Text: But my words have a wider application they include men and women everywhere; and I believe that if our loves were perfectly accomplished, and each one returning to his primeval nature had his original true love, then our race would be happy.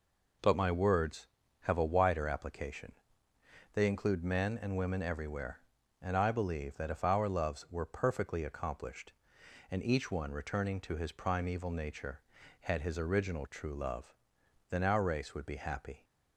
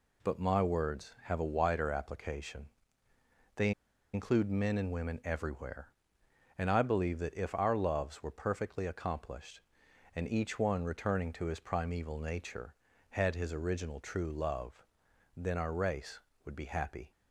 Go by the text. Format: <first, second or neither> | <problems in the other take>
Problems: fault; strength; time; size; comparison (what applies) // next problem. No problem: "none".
first | pauses between "application" and "they"; noticeable; at 2.6 s; 0.88 s long; noticeable in the first // pauses between "they" and "include"; at 3.7 s; 0.42 s long